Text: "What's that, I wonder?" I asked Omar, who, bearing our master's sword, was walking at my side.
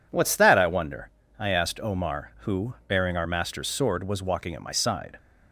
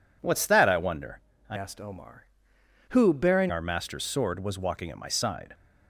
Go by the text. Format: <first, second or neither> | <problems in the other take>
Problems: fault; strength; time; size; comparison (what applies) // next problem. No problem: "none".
first | changes voice from "asked" to "bearing"; from 1.5 to 3.5 s; 2.0 s long